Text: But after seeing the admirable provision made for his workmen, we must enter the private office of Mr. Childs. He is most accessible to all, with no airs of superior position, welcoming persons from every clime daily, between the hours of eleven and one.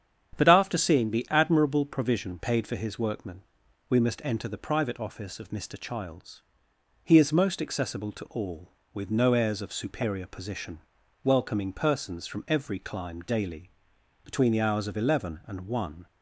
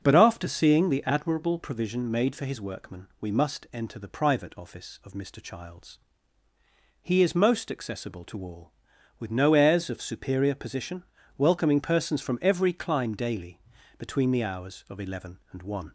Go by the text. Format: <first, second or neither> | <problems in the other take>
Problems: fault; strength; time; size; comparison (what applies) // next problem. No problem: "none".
second | starts louder than the rest; strong; until 1.3 s; 8.5 dB; noticeable in the second // says "paid" for "made"; at 2.3 s